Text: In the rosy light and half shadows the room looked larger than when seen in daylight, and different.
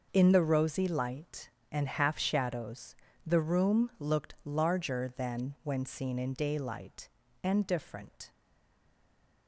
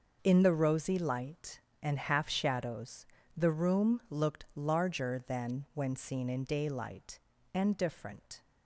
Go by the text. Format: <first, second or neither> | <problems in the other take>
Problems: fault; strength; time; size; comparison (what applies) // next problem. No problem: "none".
second | pauses between "shadows" and "the"; slight; at 2.9 s; 0.32 s long; slight in the second // stays silent after the last word; from 8.3 s on; 1.1 s long